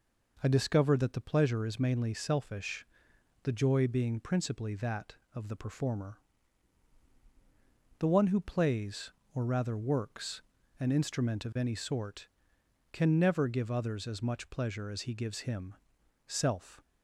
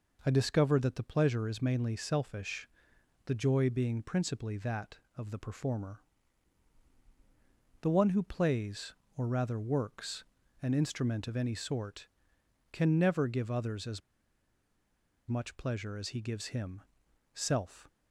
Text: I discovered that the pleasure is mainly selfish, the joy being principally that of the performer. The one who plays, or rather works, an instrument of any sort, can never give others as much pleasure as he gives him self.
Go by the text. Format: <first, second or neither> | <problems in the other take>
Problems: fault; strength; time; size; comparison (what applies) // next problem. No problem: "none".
first | pauses between "as" and "much"; strong; at 14.0 s; 1.2 s long // pauses between "him" and "self"; noticeable; at 16.8 s; 0.52 s long; noticeable in the first